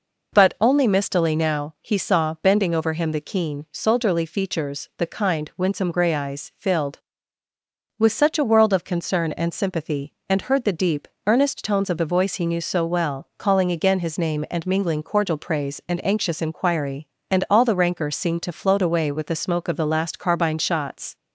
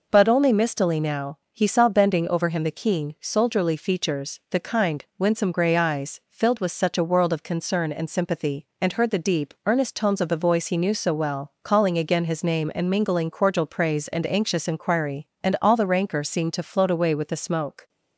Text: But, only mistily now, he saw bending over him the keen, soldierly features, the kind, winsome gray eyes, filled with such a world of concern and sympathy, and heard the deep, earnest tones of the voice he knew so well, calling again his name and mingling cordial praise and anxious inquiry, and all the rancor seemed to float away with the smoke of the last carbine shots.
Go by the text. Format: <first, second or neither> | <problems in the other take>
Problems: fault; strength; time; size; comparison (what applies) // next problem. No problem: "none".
first | stops before "of the last carbine shots"; at 17.8 s